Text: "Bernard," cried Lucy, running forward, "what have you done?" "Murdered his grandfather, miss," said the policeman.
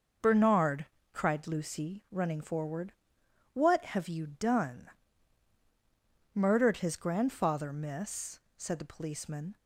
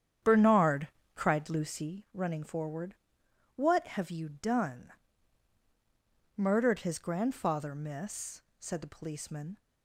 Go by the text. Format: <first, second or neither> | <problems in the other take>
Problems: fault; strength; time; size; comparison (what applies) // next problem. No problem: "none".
first | starts louder than the rest; strong; until 1.9 s; 9 dB